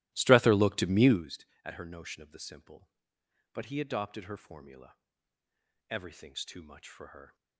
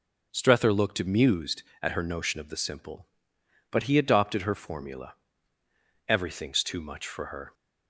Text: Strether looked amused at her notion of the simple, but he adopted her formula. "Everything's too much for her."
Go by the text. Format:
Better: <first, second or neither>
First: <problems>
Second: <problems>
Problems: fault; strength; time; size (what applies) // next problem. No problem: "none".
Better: second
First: starts louder than the rest; strong; until 1.3 s; 17 dB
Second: none